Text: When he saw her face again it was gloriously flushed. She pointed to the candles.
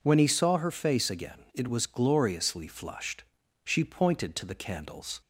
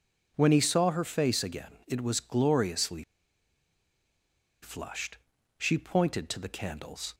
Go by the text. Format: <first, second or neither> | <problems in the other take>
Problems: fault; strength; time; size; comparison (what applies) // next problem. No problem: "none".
first | pauses between "gloriously" and "flushed"; strong; at 3.0 s; 1.5 s long